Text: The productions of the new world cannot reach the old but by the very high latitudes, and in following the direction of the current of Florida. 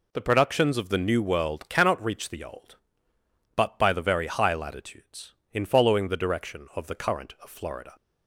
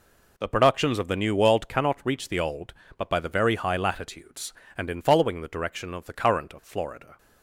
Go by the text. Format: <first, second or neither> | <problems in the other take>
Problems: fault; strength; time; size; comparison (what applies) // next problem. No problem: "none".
second | skips "and"; at 5.4 s